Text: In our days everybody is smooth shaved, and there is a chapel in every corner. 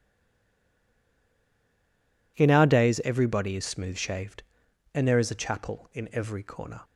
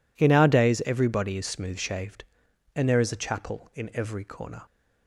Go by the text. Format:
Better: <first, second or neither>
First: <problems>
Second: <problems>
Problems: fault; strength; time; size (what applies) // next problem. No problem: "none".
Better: second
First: stays silent before the first word; until 2.3 s; 2.3 s long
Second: none